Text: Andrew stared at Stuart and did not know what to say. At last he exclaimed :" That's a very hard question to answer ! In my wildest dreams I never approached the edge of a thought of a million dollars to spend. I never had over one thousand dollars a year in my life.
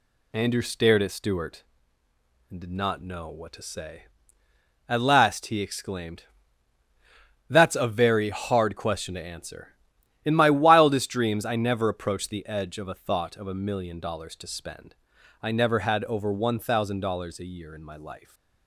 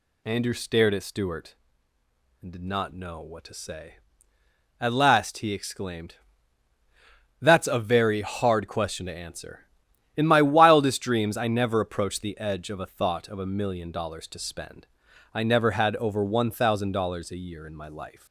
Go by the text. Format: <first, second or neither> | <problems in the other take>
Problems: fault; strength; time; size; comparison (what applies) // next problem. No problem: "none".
first | gets louder; slight; throughout; 2.5 dB